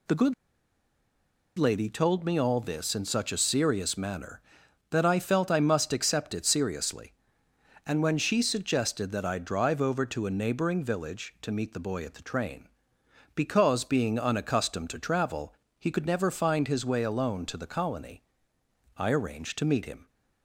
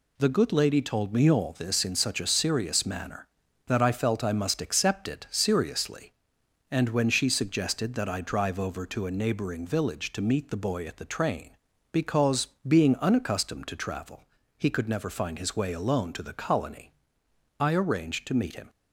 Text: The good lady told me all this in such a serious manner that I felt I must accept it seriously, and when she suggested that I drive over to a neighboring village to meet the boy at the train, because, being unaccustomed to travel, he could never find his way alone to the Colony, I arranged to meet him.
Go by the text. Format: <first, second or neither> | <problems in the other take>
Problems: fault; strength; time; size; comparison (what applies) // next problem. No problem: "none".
second | pauses between "good" and "lady"; at 0.3 s; 1.2 s long